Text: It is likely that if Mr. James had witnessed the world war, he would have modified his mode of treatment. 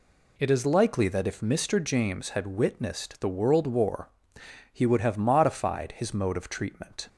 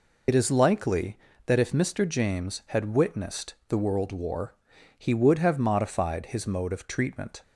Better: first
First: none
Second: loses the start of "It"; at 0.2 s; 60 ms

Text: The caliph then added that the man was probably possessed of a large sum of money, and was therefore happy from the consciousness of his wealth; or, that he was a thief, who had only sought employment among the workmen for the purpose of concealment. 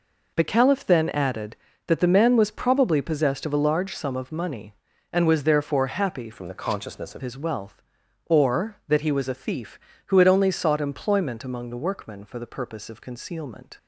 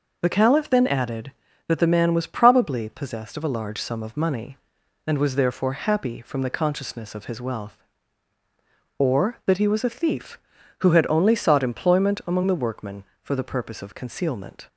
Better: second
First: changes voice from "from" to "of"; from 6.3 to 7.2 s; 0.9 s long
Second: none

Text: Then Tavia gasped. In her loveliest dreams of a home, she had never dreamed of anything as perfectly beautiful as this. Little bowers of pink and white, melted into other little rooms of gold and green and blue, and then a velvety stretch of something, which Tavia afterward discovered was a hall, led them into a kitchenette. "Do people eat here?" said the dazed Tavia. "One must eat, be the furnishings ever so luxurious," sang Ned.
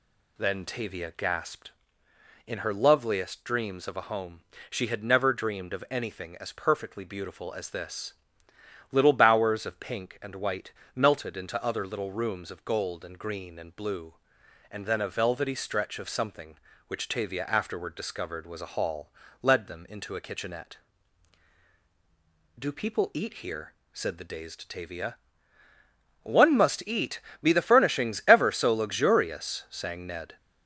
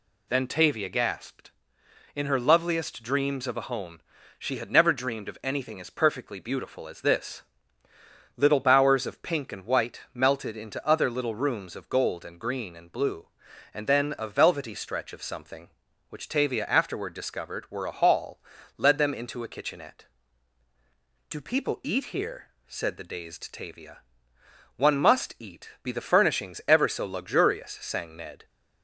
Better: first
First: none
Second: says "were" for "was"; at 17.6 s

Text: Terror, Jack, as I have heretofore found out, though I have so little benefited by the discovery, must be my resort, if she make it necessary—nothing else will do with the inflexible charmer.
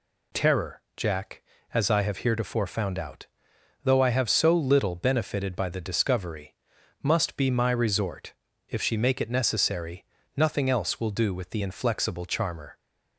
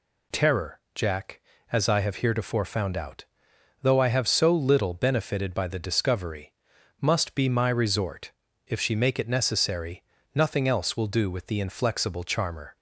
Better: neither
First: none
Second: none

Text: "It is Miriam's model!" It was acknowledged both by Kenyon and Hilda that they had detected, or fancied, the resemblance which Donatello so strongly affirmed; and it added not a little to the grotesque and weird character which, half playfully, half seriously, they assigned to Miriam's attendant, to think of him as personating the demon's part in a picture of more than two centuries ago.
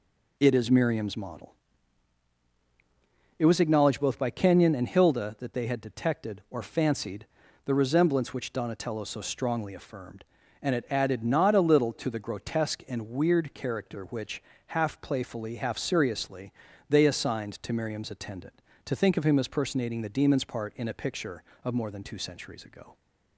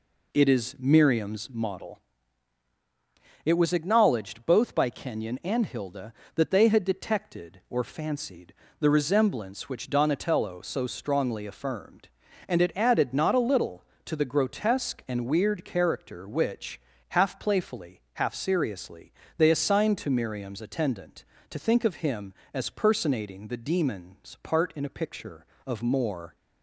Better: first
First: none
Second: stops before "than two centuries ago"; at 26.3 s

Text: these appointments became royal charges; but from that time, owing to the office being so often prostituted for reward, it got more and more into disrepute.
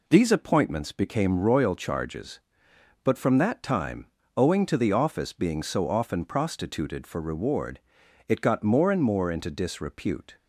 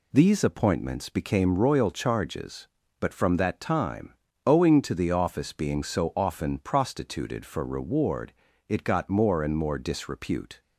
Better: first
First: none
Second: skips "into"; at 9.7 s

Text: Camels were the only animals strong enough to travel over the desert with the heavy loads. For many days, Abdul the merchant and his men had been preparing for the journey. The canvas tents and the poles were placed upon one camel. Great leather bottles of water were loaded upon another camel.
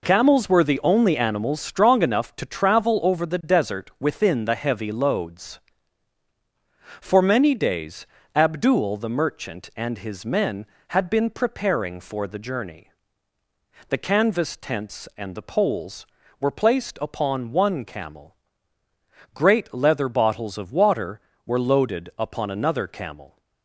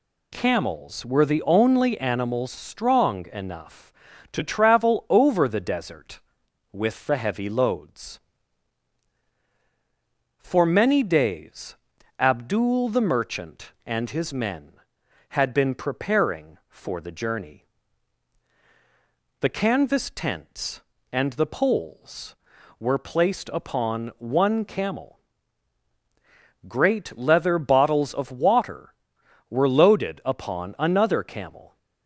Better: second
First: says "within" for "with"; at 3.9 s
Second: none

